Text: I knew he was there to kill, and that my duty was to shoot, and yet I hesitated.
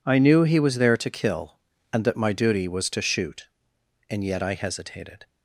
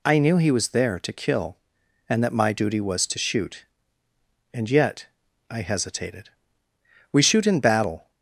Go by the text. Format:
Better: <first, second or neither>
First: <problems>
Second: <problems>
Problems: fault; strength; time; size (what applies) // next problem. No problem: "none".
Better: first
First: none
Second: pauses between "yet" and "I"; at 5.0 s; 0.44 s long // goes on to say "We shoot in battle"; noticeable; from 7.1 s on; 0.98 s long